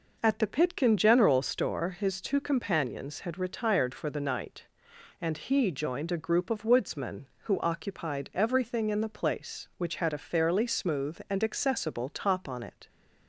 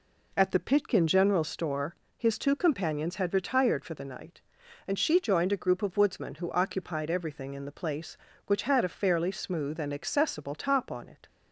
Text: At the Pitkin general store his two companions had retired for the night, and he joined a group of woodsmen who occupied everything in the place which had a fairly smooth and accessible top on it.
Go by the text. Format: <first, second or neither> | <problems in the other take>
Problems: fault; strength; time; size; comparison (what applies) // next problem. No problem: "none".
first | pauses between "store" and "his"; slight; at 1.9 s; 0.22 s long // says "she" for "he"; at 4.9 s